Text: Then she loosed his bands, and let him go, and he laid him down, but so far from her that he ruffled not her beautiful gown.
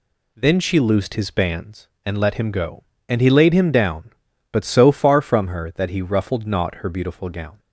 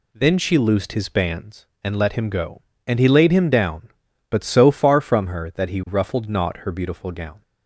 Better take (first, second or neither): neither